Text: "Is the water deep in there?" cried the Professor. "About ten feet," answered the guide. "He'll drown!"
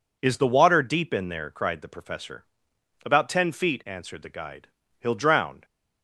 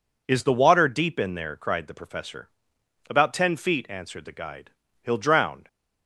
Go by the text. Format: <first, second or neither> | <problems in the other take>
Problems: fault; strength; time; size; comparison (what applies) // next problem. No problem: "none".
neither | none